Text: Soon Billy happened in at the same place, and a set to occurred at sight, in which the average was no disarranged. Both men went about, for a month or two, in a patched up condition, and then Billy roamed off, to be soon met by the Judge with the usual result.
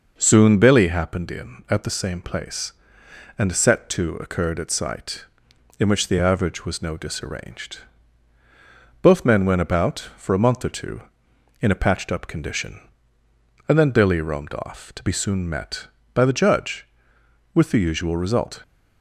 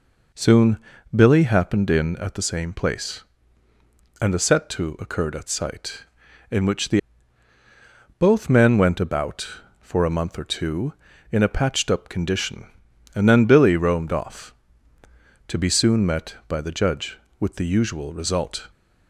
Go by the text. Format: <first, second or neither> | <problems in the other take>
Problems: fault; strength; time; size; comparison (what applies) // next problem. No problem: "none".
first | pauses between "Soon" and "Billy"; slight; at 0.7 s; 0.36 s long // skips "average was no disarranged"; at 7.5 s